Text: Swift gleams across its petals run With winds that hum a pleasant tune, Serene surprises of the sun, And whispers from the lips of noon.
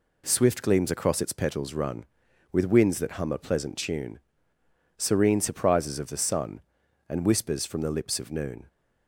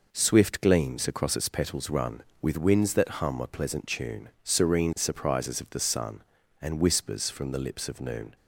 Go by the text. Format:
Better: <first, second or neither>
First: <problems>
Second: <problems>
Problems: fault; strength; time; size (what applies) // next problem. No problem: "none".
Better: neither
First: none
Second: none